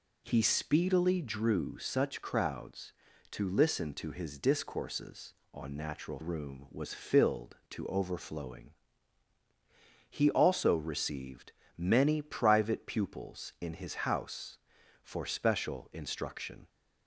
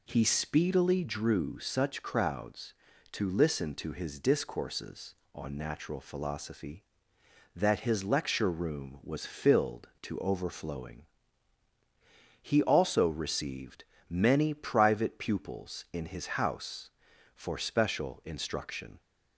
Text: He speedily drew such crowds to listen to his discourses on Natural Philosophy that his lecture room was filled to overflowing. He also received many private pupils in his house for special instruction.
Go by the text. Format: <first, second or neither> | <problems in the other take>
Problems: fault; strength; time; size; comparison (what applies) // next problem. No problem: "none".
second | skips "Philosophy that his lecture"; at 6.1 s // pauses between "received" and "many"; slight; at 11.4 s; 0.26 s long; slight in the second